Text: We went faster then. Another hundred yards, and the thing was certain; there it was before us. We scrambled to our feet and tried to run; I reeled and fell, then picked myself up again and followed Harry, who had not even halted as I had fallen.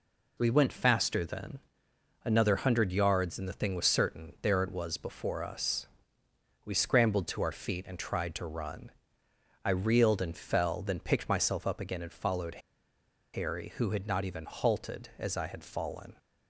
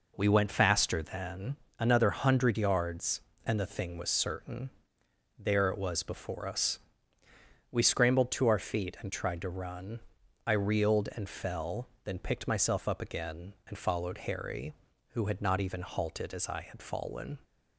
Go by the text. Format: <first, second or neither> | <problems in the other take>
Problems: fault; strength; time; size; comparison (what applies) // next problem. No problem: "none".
second | pauses between "followed" and "Harry"; noticeable; at 12.6 s; 0.74 s long